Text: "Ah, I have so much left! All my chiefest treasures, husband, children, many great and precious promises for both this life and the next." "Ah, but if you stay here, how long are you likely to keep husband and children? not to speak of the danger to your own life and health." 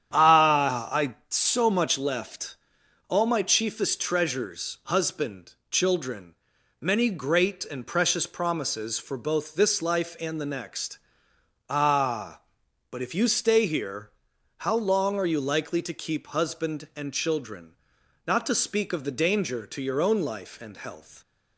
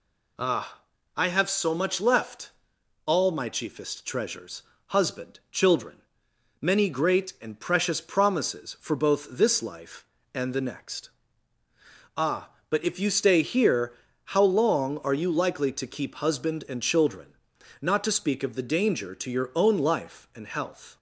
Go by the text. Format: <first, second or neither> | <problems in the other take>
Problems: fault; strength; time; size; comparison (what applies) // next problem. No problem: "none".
second | starts louder than the rest; strong; until 1.1 s; 9.5 dB // skips "have"; at 1.2 s